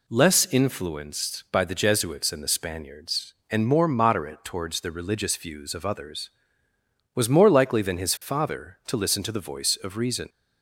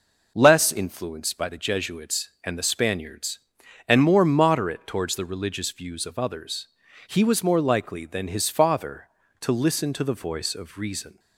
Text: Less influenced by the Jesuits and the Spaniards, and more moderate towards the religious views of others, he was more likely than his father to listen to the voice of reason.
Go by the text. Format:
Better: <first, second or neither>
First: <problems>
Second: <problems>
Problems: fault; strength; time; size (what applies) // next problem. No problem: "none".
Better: second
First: skips "he"; at 6.7 s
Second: none